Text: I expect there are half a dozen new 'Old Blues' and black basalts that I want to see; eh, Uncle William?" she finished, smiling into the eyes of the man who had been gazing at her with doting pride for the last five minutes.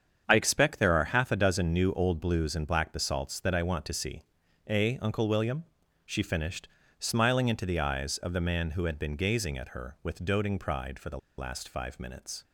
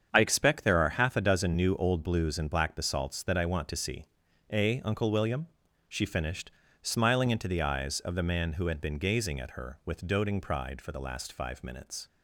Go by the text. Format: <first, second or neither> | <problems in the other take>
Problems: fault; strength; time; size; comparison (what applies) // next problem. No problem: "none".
second | starts louder than the rest; strong; until 1.2 s; 7.5 dB; strong in the second // pauses between "the" and "last"; slight; at 11.1 s; 0.19 s long